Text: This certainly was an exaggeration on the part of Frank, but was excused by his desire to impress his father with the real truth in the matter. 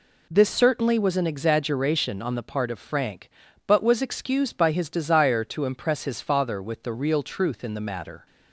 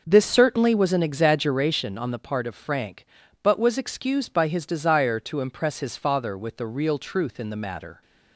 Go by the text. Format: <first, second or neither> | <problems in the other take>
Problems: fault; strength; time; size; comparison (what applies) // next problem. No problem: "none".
first | starts louder than the rest; noticeable; until 1.8 s; 5.5 dB